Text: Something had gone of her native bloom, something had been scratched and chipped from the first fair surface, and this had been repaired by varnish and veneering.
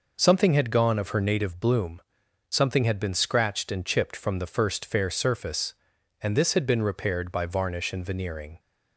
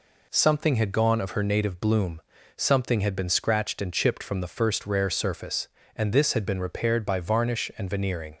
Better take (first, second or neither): first